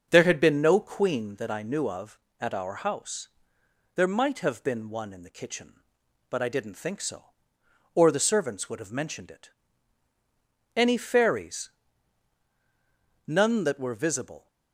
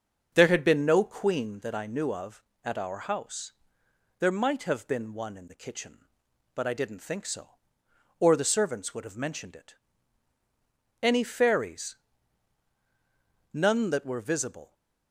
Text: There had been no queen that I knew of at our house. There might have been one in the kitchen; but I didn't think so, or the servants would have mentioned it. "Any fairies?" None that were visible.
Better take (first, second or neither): neither